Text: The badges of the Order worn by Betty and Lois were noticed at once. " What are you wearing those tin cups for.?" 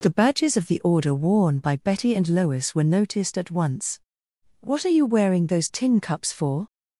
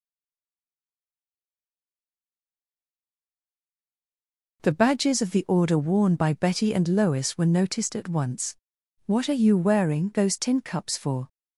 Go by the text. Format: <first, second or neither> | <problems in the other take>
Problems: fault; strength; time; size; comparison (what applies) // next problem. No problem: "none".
first | stays silent before the first word; strong; until 4.6 s; 4.6 s long